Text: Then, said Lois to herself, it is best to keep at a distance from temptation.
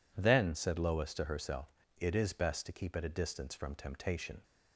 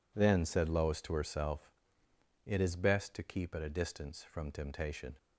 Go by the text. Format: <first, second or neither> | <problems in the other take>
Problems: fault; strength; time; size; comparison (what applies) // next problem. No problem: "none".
neither | none